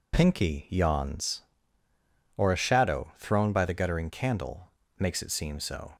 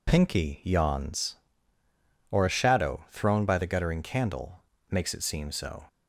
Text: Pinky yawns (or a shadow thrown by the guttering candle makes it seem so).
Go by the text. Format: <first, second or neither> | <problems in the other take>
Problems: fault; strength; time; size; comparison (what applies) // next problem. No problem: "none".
neither | pauses between "candle" and "makes"; slight; the same in both